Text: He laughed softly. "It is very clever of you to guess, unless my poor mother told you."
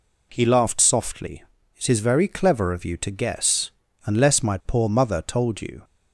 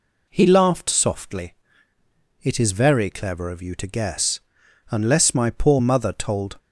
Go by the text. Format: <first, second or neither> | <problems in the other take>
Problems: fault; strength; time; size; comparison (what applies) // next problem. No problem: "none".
first | stops before "you"; at 6.5 s